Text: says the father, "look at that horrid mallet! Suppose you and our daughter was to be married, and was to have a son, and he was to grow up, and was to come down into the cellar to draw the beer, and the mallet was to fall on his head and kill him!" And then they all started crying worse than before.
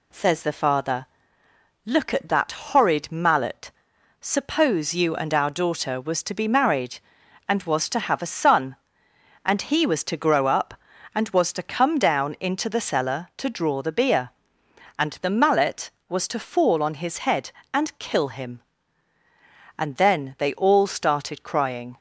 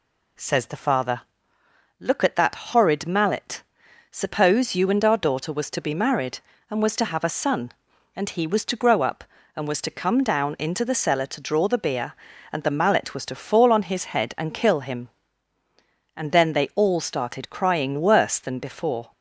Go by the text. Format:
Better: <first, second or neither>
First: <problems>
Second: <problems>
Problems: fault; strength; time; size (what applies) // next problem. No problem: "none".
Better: second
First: stops before "worse than before"; at 21.9 s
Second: none